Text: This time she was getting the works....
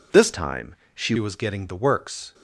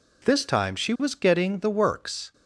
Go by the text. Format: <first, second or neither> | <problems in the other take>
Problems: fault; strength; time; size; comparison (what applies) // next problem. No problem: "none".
second | changes voice from "time" to "she"; from 0.3 to 1.1 s; 0.8 s long // pauses between "time" and "she"; slight; at 0.7 s; 0.18 s long